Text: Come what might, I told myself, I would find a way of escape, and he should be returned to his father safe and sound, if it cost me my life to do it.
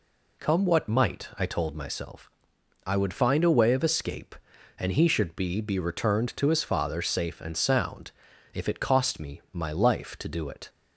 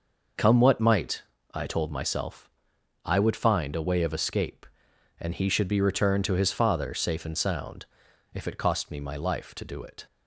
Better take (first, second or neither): second